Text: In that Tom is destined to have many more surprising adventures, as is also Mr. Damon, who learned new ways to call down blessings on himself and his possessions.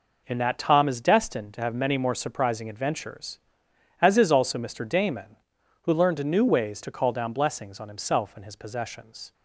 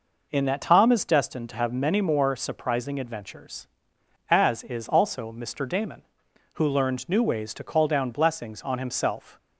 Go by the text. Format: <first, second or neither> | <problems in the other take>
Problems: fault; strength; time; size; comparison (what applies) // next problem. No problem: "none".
first | stops before "and his possessions"; at 9.3 s